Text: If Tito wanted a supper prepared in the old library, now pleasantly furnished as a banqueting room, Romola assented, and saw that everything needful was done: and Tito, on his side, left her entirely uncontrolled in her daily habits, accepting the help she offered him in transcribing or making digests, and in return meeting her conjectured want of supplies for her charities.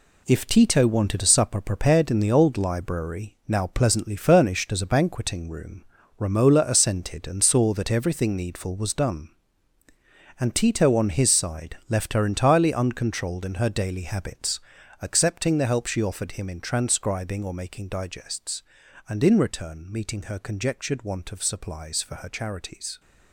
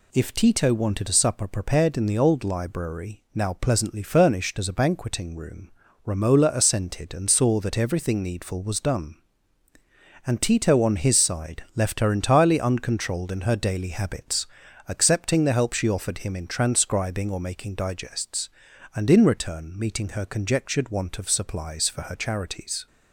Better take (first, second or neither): second